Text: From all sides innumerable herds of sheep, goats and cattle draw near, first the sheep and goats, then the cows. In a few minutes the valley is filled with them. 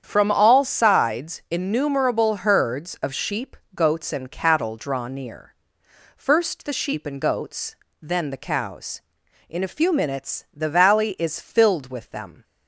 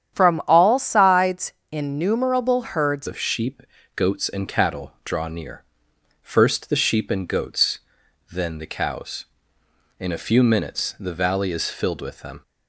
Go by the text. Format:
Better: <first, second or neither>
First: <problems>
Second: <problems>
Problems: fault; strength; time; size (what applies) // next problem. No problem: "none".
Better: first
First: starts louder than the rest; strong; until 1.0 s; 8.5 dB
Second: starts louder than the rest; strong; until 1.2 s; 9.5 dB // pauses between "sides" and "innumerable"; slight; at 1.5 s; 0.18 s long // changes voice at "of"; from 3.0 s on; 9.4 s long